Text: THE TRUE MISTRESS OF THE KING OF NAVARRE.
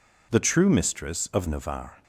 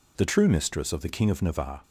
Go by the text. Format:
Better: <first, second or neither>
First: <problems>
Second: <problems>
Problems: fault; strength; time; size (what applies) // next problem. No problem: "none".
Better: second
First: skips "THE KING OF"; at 1.4 s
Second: none